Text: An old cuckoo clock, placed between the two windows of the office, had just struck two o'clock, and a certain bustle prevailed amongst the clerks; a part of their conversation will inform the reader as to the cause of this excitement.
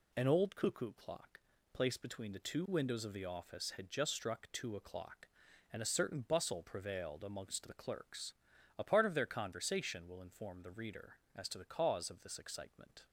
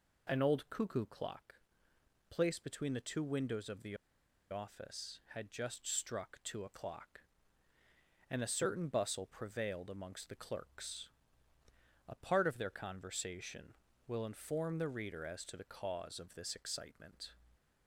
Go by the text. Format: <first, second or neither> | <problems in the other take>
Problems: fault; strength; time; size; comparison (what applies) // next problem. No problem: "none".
first | pauses between "the" and "office"; noticeable; at 3.9 s; 0.54 s long